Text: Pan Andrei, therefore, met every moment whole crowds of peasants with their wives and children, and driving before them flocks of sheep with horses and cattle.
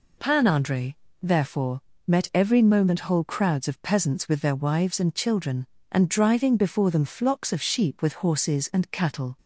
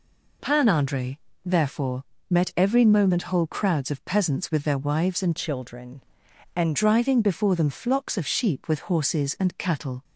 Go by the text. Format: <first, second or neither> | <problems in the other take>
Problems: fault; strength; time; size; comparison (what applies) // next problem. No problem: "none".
first | changes voice from "children" to "and"; from 5.3 to 6.7 s; 1.4 s long